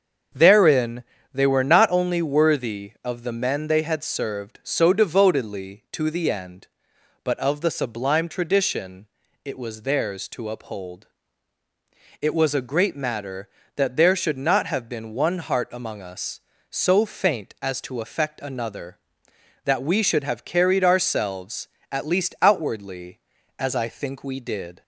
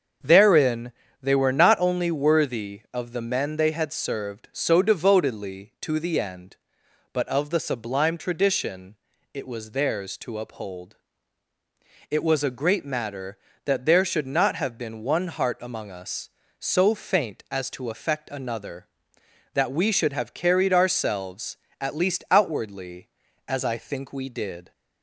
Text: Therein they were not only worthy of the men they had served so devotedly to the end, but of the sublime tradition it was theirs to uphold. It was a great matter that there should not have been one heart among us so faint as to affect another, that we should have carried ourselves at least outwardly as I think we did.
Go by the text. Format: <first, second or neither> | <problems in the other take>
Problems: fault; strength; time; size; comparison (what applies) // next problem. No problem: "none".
neither | starts louder than the rest; the same in both // pauses between "Therein" and "they"; slight; the same in both // pauses between "tradition" and "it"; the same in both